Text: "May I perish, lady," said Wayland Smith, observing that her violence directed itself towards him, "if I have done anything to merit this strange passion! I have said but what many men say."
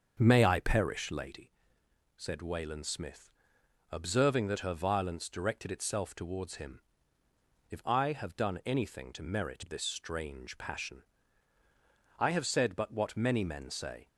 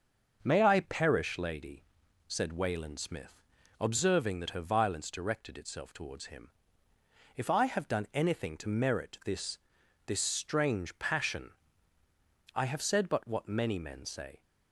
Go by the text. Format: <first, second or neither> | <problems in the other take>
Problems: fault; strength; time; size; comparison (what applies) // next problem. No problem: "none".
first | starts louder than the rest; until 1.4 s; 6 dB; also in the first // says "this" twice; at 10.0 s